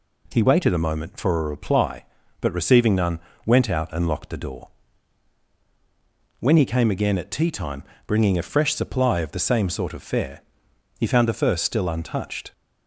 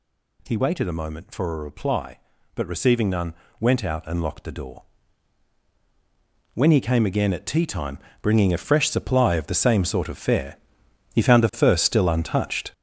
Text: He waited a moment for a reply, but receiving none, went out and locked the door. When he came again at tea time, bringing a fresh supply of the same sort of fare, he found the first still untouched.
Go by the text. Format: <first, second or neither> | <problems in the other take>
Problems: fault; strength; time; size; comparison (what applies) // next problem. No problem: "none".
first | gets louder; strong; throughout; 7.5 dB